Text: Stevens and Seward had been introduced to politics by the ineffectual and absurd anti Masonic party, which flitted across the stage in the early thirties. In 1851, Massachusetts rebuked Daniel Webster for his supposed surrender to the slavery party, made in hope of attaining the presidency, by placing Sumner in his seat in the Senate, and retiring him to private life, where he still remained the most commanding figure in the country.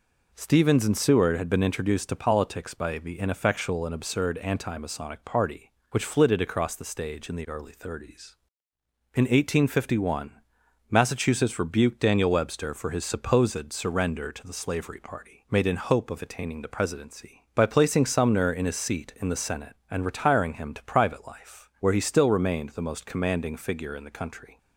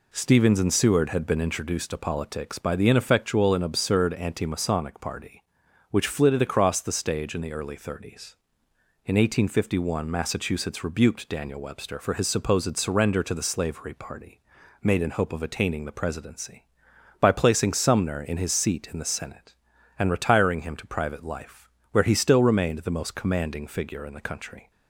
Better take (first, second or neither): neither